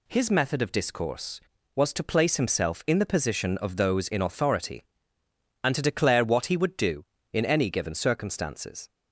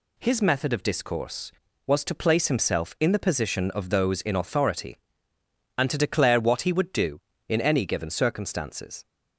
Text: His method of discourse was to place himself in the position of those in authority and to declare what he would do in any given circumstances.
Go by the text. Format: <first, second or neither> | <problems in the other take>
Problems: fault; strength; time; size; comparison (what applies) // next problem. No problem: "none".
neither | none